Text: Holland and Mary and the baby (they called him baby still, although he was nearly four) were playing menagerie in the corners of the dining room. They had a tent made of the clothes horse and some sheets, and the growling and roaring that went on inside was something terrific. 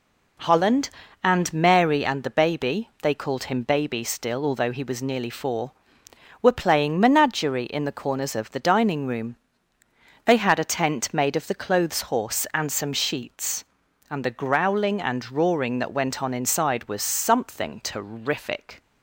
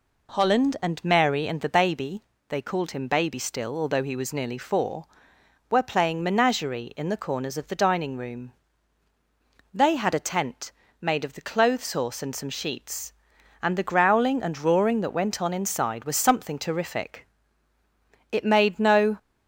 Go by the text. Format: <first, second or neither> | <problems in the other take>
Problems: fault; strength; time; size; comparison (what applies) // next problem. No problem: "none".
first | pauses between "tent" and "made"; slight; at 10.6 s; 0.32 s long // goes on to say "It made no"; noticeable; from 18.2 s on; 0.88 s long